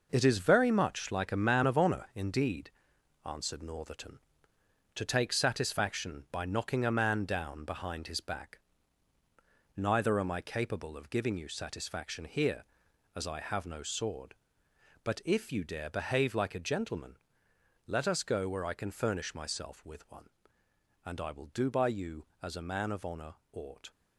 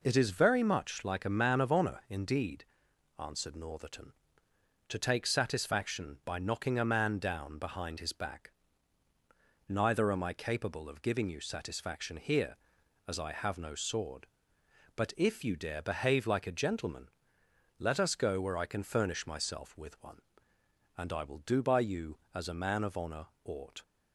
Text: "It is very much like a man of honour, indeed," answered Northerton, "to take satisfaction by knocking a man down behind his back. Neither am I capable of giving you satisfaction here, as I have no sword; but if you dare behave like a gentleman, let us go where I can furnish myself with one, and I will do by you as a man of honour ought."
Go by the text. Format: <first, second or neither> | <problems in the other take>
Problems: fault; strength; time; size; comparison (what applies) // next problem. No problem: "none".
second | gets quieter; strong; throughout; 8 dB // pauses between "honour" and "ought"; slight; at 23.3 s; 0.18 s long; slight in the second